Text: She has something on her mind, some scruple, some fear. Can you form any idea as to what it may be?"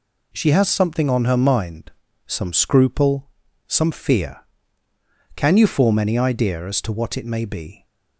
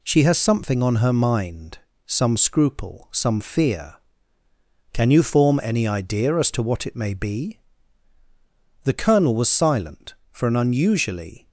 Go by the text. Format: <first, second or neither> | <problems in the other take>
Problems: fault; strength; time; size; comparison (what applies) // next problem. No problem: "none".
first | goes on to say "The Colonel was silent for an unusually"; strong; from 8.8 s on; 2.6 s long